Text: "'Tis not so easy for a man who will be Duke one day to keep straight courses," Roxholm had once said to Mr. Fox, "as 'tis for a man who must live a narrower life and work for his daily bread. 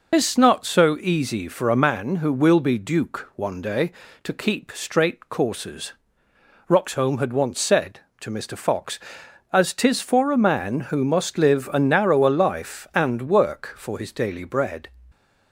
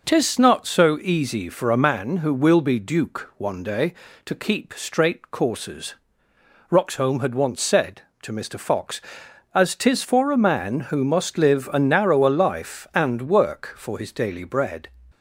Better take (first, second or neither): second